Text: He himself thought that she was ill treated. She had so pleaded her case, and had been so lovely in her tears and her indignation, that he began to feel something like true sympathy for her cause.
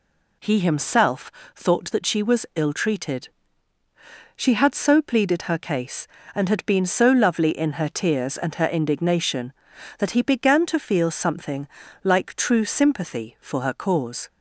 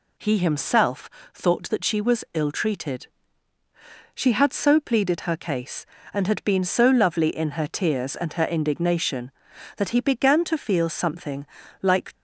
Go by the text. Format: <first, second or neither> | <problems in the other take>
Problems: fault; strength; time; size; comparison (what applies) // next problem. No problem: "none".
first | pauses between "himself" and "thought"; slight; at 1.0 s; 0.24 s long; slight in the first // pauses between "something" and "like"; at 11.4 s; 0.38 s long; also in the first // stops before "true sympathy for her cause"; at 12.1 s